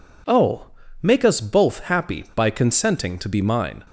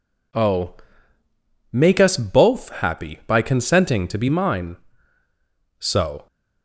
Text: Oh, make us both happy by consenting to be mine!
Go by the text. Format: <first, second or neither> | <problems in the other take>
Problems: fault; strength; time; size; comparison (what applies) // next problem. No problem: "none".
first | goes on to say "So"; slight; from 5.7 s on; 0.48 s long